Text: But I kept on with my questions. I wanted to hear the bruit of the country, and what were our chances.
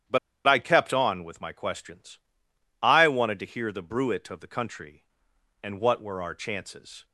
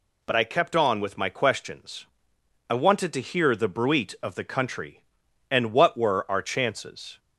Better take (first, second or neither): second